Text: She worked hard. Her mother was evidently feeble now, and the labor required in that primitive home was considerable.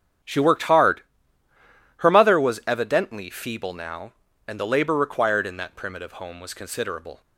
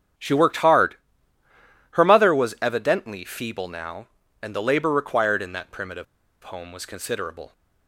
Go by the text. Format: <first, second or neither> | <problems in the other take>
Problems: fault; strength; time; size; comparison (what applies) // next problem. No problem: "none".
first | starts louder than the rest; strong; until 2.1 s; 8.5 dB; strong in the first // pauses between "primitive" and "home"; at 6.0 s; 0.39 s long